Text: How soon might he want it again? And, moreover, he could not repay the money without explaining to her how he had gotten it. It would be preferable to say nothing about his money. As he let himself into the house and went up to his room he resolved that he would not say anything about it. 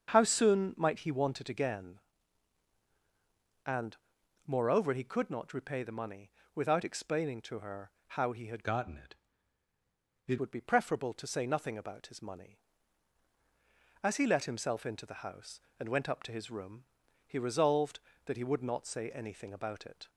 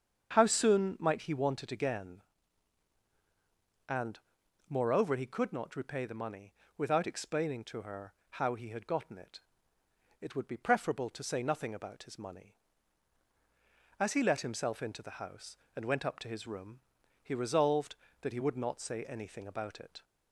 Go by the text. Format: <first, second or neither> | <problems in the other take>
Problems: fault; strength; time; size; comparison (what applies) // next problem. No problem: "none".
second | starts louder than the rest; strong; until 1.1 s; 7.5 dB; strong in the second // pauses between "money" and "without"; slight; at 6.3 s; 0.24 s long; slight in the second // pauses between "her" and "how"; slight; at 7.9 s; 0.16 s long; slight in the second // changes voice from "gotten" to "It"; from 8.6 to 10.3 s; 1.7 s long // pauses between "room" and "he"; at 16.8 s; 0.42 s long; also in the second